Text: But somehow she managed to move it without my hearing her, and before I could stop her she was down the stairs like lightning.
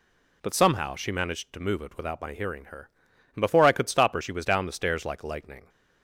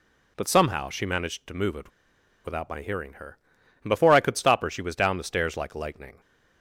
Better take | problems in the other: first | pauses between "it" and "without"; noticeable; at 1.8 s; 0.56 s long

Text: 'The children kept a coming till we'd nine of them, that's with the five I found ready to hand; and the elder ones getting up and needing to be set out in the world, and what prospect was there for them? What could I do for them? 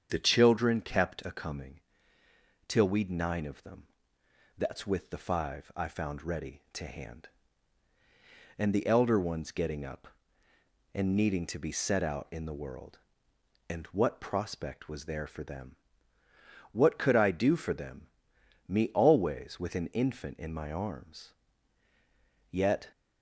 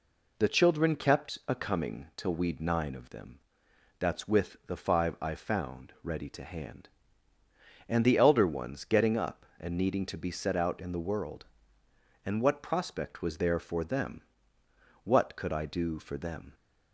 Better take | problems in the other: second | starts louder than the rest; strong; until 1.1 s; 7.5 dB // pauses between "coming" and "till"; noticeable; at 1.7 s; 0.88 s long // goes on to say "Me always with an infant in my arms Yet"; strong; from 18.6 s on; 4.2 s long

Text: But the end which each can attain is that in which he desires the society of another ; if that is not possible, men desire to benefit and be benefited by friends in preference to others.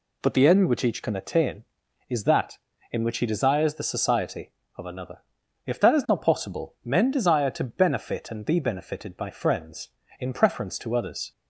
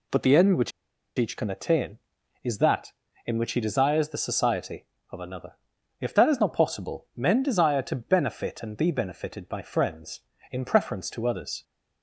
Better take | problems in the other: first | pauses between "which" and "each"; noticeable; at 0.7 s; 0.48 s long

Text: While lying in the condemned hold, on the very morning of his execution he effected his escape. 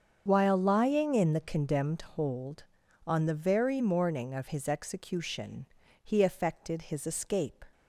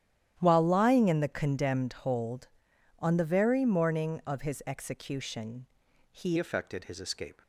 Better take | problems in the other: first | starts louder than the rest; strong; until 1.4 s; 11.5 dB; also in the first // pauses between "execution" and "he"; noticeable; at 5.6 s; 0.46 s long; slight in the first // changes voice at "effected"; from 6.3 s on; 1.1 s long

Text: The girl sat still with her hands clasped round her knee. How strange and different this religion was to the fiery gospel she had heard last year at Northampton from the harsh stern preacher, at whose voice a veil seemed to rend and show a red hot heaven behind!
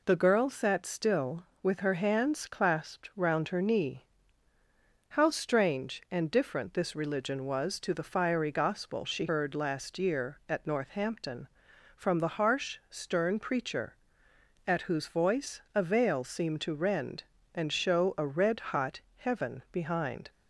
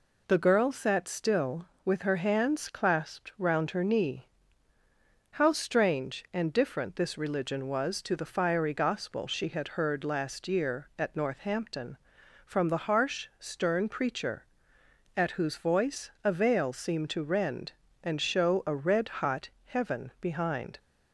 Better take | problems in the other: second | skips "had"; at 9.2 s // pauses between "hot" and "heaven"; slight; at 19.0 s; 0.16 s long; slight in the second

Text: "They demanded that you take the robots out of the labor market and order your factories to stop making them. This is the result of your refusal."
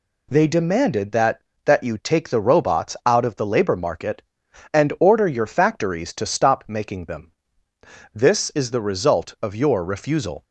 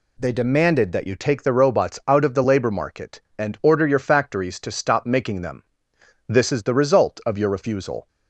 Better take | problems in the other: second | says "that" twice; at 1.6 s

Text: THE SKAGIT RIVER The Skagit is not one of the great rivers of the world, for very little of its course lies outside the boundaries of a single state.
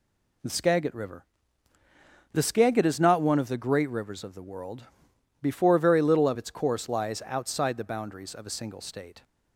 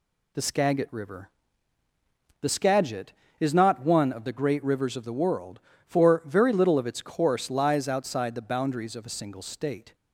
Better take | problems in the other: second | pauses between "RIVER" and "The"; at 1.2 s; 1.0 s long; also in the second // says "before" for "for"; at 5.4 s

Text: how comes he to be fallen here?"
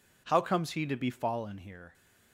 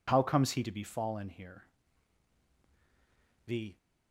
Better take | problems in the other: first | goes on to say "The"; slight; from 3.4 s on; 0.32 s long

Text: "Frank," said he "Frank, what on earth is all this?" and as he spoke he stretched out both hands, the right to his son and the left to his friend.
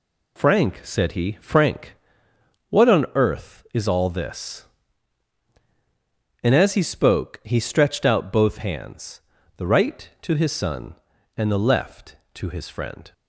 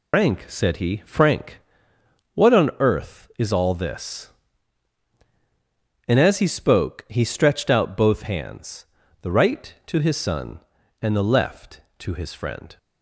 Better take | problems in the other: first | loses the start of "Frank"; at 0.1 s; 130 ms

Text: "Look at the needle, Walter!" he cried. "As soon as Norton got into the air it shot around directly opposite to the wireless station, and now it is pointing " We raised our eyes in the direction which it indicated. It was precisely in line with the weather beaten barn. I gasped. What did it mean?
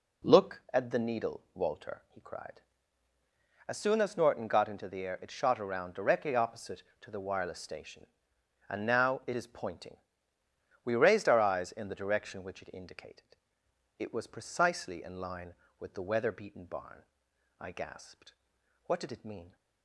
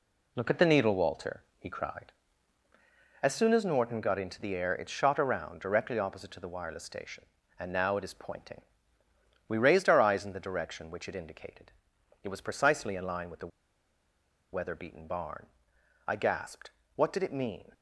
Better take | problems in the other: first | pauses between "the" and "weather"; at 13.5 s; 1.0 s long

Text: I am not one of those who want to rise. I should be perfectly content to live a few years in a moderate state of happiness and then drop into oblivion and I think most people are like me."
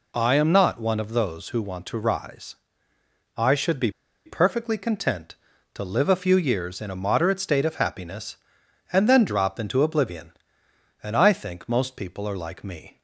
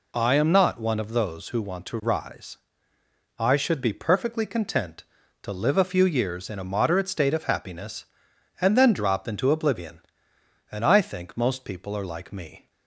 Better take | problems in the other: second | pauses between "be" and "perfectly"; slight; at 3.9 s; 0.33 s long

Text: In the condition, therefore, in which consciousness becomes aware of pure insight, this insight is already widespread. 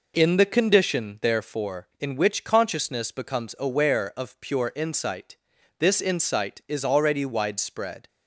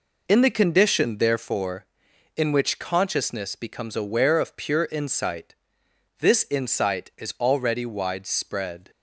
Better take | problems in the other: neither | none

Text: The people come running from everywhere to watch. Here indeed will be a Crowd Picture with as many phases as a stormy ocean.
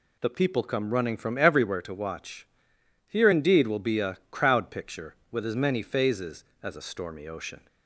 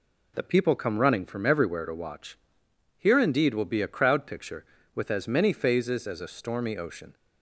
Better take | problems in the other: neither | none

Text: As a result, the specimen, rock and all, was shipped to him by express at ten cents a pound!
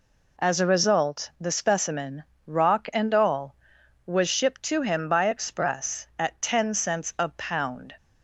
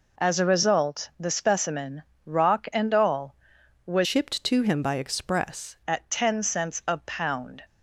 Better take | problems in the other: first | changes voice from "shipped" to "express"; from 4.0 to 5.7 s; 1.7 s long

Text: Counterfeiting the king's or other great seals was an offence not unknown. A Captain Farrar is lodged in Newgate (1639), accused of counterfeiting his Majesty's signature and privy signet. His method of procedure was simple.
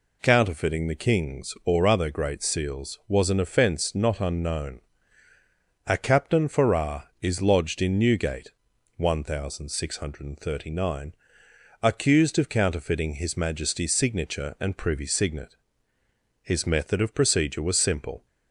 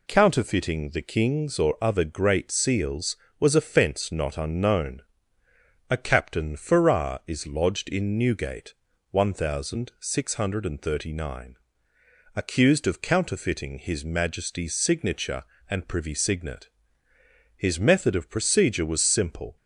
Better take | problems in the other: first | skips "an"; at 3.5 s

